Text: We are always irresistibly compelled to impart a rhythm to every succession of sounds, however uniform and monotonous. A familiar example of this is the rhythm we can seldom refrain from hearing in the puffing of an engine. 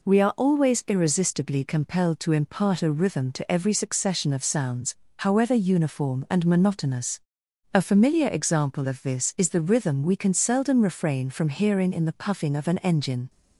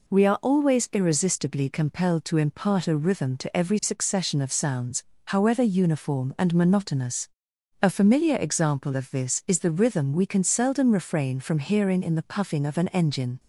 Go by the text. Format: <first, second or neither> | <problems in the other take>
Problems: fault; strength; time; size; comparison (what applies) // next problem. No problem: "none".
neither | none